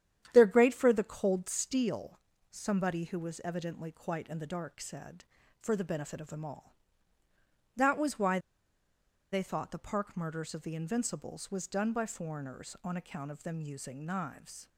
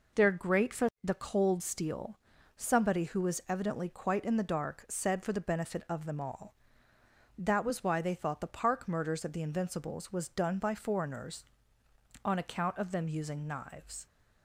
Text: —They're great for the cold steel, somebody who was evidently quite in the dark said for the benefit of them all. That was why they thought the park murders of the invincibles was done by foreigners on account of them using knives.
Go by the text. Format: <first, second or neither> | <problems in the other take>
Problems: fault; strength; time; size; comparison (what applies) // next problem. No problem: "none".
second | starts louder than the rest; strong; until 1.3 s; 10 dB // pauses between "why" and "they"; noticeable; at 8.3 s; 0.93 s long